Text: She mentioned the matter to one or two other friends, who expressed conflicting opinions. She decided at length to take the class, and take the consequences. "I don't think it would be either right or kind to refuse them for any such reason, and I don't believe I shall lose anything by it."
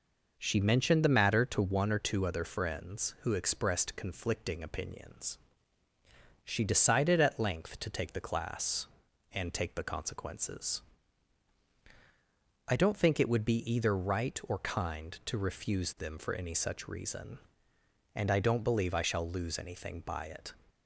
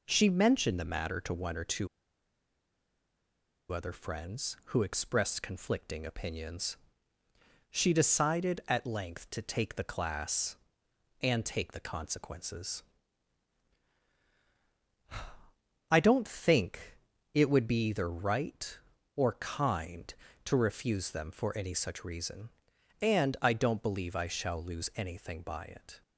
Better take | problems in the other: first | pauses between "two" and "other"; strong; at 1.8 s; 1.8 s long // pauses between "think" and "it"; slight; at 16.9 s; 0.34 s long

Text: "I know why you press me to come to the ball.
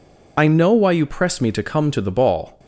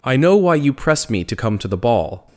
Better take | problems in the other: second | loses the start of "I"; at 0.3 s; 25 ms

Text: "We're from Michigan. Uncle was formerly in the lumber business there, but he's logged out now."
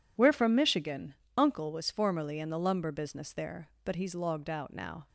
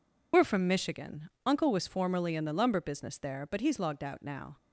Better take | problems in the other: first | loses the start of "We're"; at 0.3 s; 50 ms

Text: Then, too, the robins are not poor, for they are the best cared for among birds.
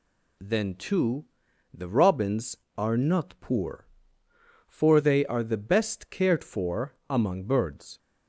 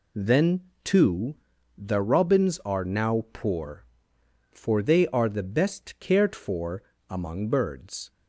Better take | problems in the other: first | says "now" for "not"; at 2.8 s // pauses between "for" and "among"; slight; at 6.8 s; 0.25 s long; slight in the first

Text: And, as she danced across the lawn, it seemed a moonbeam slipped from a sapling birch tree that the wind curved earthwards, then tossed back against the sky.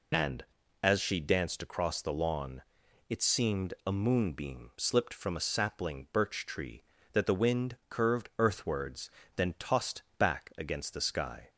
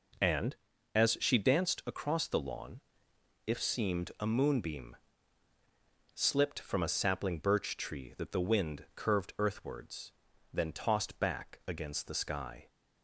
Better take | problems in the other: first | says "if" for "it"; at 3.4 s // pauses between "moonbeam" and "slipped"; at 4.9 s; 1.1 s long

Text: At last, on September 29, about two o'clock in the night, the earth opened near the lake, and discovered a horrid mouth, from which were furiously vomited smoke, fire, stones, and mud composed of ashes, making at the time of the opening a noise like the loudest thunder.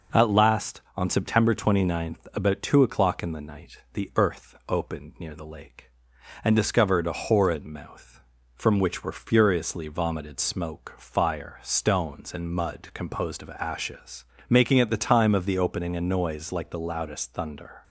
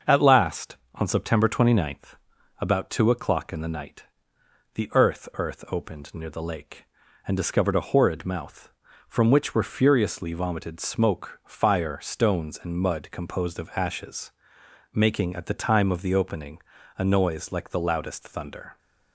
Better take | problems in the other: first | starts louder than the rest; until 1.2 s; 6.5 dB // says "earth" twice; at 5.3 s // pauses between "opening" and "a"; at 16.5 s; 0.40 s long

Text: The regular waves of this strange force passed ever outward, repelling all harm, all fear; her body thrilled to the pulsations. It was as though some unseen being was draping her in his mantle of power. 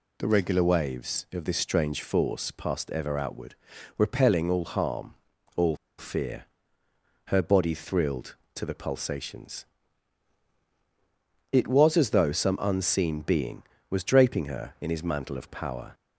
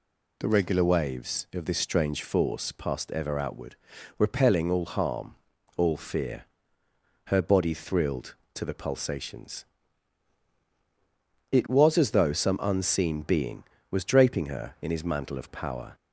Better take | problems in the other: second | pauses between "all" and "fear"; slight; at 5.7 s; 0.23 s long

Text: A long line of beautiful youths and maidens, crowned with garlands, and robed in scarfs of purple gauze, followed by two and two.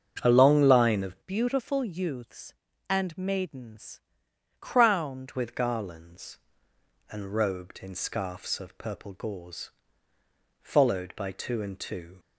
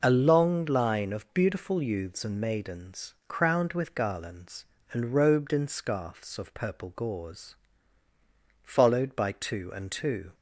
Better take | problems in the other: second | starts louder than the rest; until 1.2 s; 7 dB // changes voice from "beautiful" to "crowned"; from 1.2 to 5.3 s; 4.1 s long

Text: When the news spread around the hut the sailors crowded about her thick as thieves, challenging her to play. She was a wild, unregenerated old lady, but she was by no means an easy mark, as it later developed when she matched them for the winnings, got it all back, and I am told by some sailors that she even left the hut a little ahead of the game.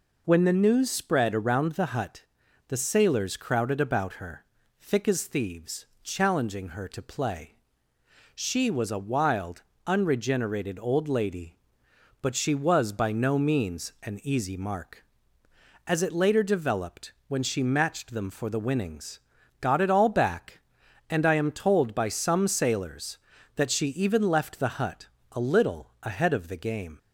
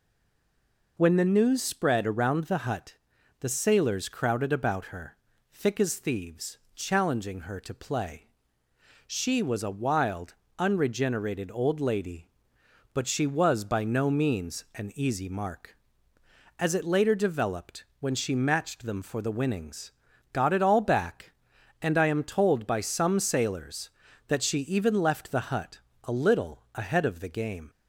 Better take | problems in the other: first | stays silent before the first word; until 0.9 s; 0.9 s long // pauses between "hut" and "the"; at 2.9 s; 0.44 s long; also in the first // pauses between "her" and "thick"; at 5.1 s; 0.38 s long; also in the first // pauses between "developed" and "when"; slight; at 17.8 s; 0.16 s long; slight in the first // pauses between "hut" and "a"; slight; at 25.7 s; 0.28 s long; slight in the first

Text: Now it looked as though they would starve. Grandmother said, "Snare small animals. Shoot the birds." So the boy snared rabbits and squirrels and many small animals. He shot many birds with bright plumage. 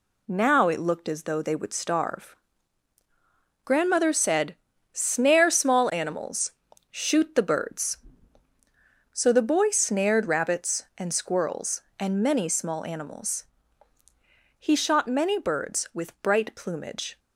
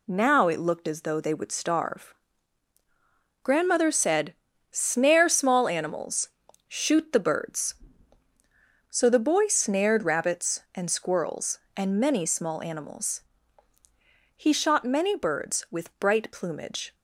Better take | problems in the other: neither | none

